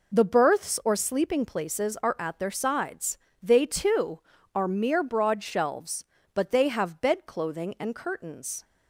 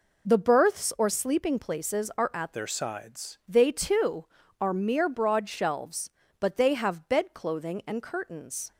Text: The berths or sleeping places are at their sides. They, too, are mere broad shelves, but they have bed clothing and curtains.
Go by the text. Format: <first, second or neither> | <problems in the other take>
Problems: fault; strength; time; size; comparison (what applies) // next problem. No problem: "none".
first | changes voice from "their" to "sides"; from 2.5 to 3.3 s; 0.8 s long